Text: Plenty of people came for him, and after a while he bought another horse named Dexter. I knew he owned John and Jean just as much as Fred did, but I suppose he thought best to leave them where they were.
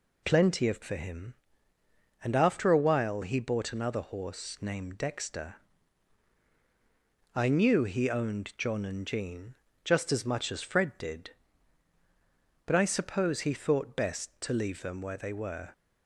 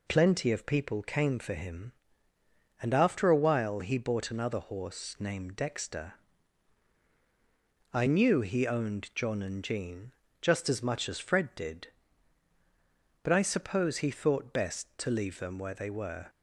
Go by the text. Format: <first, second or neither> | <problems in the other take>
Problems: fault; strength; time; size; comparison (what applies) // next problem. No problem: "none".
second | skips "people came"; at 0.8 s // pauses between "Jean" and "just"; slight; at 9.5 s; 0.28 s long; slight in the second